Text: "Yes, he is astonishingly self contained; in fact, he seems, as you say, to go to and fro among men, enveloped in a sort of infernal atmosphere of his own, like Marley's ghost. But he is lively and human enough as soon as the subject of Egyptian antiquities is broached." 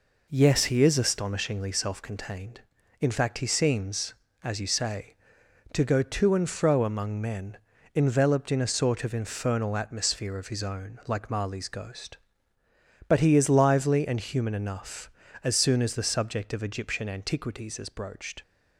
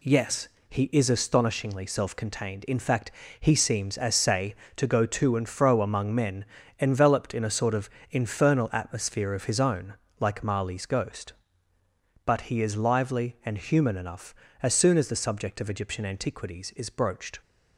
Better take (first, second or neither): first